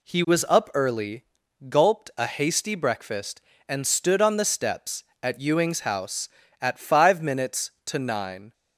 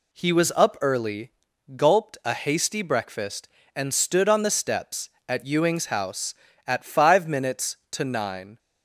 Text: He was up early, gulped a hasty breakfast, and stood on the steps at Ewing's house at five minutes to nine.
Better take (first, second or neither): neither